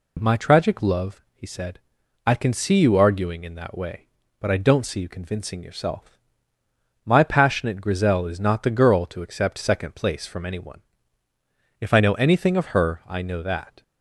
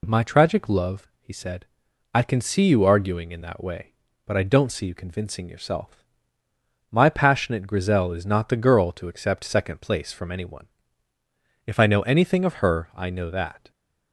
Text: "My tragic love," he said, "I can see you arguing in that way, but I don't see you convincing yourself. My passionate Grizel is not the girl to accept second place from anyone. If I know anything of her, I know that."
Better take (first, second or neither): neither